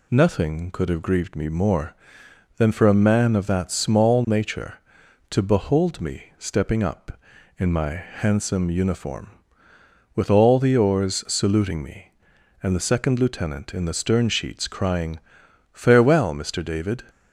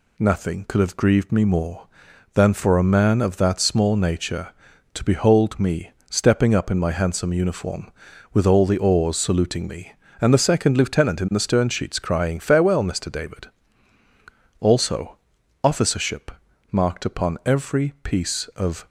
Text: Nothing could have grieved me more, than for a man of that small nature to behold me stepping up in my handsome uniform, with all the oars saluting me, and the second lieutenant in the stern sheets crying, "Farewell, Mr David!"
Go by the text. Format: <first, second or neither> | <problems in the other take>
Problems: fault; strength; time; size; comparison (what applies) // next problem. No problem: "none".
first | pauses between "me" and "stepping"; slight; at 5.9 s; 0.18 s long // goes on to say "also officership marked upon every piece of"; strong; from 14.5 s on; 4.2 s long